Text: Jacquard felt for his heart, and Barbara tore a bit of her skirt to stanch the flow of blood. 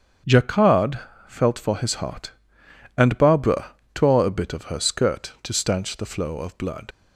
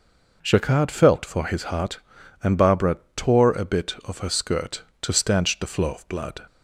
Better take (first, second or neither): second